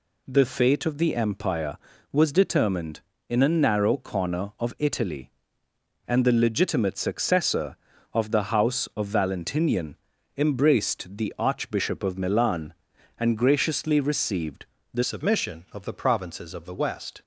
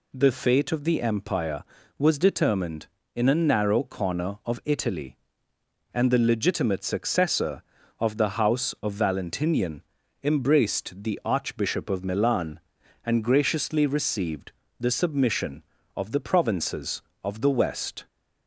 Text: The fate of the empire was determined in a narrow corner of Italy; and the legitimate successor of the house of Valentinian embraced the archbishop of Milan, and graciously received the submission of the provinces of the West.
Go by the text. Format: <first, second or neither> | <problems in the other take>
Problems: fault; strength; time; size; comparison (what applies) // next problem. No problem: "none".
second | pauses between "Valentinian" and "embraced"; at 9.9 s; 0.40 s long; also in the second // pauses between "received" and "the"; slight; at 14.6 s; 0.28 s long; slight in the second // changes voice at "submission"; from 15.0 s on; 2.2 s long